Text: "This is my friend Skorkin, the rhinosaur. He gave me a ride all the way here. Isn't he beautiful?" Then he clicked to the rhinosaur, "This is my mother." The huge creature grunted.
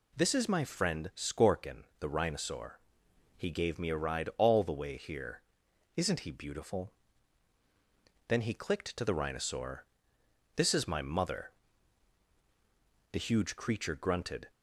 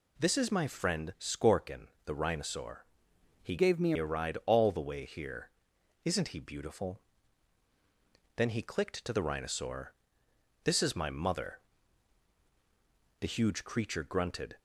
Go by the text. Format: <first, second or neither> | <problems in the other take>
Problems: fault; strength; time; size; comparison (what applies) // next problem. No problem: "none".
first | changes voice from "gave" to "me"; from 3.5 to 3.9 s; 0.4 s long